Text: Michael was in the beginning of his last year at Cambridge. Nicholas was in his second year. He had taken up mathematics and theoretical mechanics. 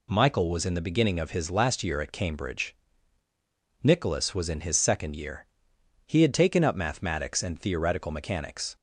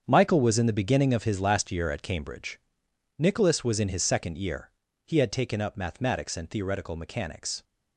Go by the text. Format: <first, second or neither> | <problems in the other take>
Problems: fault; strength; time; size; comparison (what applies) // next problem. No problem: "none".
first | gets quieter; strong; throughout; 11 dB